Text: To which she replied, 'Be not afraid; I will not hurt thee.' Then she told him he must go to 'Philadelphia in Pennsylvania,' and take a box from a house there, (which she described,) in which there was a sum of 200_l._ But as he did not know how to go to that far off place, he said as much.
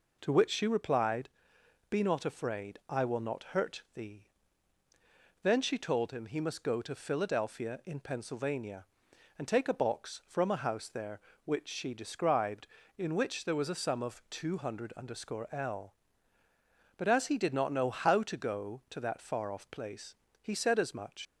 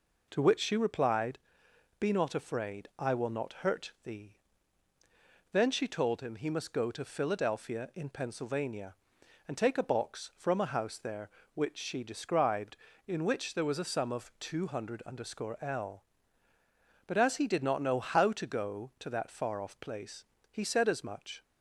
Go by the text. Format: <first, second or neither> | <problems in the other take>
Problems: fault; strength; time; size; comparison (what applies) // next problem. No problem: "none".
second | leaves "much" unfinished; at 21.2 s; 75 ms